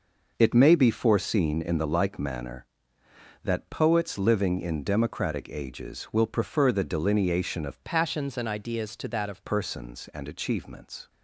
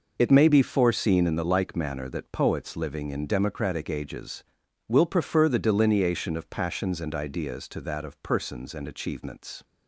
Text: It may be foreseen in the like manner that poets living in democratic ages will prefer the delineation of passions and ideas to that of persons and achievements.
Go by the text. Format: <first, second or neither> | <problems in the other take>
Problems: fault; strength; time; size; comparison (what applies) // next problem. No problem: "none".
second | changes voice from "passions" to "of"; from 7.8 to 9.4 s; 1.6 s long